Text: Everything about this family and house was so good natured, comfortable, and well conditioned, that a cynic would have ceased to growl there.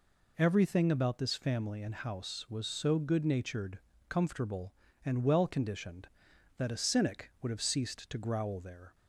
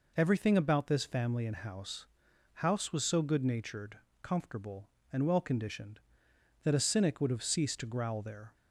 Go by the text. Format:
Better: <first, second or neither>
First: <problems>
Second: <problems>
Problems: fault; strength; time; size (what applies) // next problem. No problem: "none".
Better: first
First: none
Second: says "house" twice; at 2.5 s